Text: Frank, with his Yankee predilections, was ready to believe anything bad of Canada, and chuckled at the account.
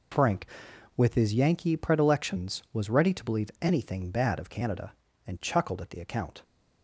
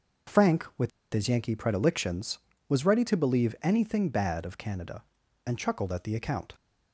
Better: first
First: none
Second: pauses between "with" and "his"; slight; at 0.9 s; 0.23 s long

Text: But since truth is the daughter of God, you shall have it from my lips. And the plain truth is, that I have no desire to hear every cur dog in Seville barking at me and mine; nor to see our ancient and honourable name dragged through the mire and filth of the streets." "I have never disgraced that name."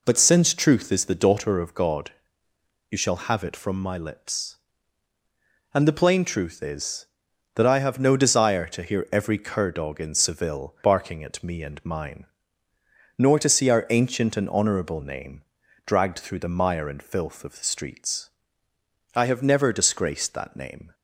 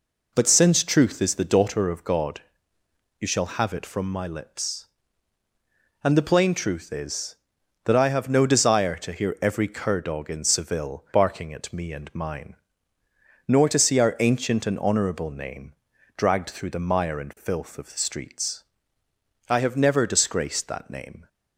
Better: neither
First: pauses between "name" and "dragged"; at 15.4 s; 0.44 s long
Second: pauses between "name" and "dragged"; at 15.7 s; 0.44 s long

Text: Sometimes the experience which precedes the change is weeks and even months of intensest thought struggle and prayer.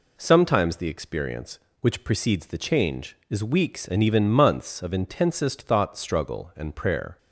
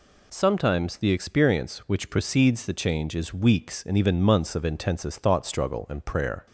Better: neither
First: none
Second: none

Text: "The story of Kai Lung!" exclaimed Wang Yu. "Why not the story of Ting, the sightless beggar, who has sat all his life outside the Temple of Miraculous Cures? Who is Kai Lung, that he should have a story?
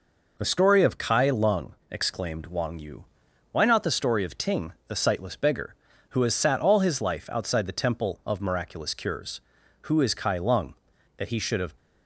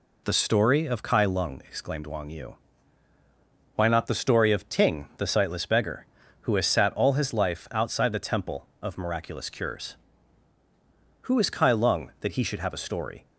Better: second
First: stops before "a story"; at 11.7 s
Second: none

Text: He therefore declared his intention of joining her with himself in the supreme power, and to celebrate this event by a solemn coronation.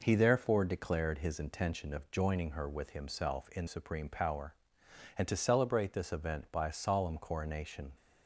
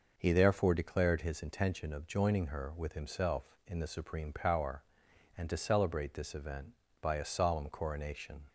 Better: second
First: skips "the"; at 3.6 s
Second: none

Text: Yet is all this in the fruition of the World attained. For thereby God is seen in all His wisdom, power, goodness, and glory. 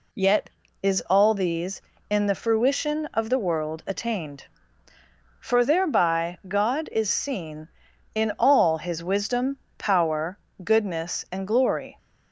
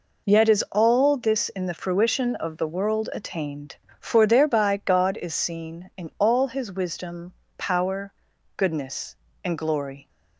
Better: second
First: says "these" for "this"; at 1.3 s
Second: none

